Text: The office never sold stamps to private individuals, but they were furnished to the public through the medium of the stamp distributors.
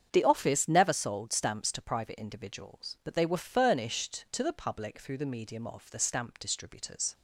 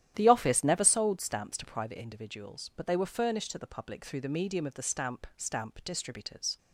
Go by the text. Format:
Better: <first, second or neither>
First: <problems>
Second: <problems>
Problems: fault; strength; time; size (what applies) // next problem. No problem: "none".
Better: first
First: starts louder than the rest; strong; until 1.1 s; 7.5 dB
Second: starts louder than the rest; strong; until 1.1 s; 11.5 dB // says "stamp" twice; at 5.3 s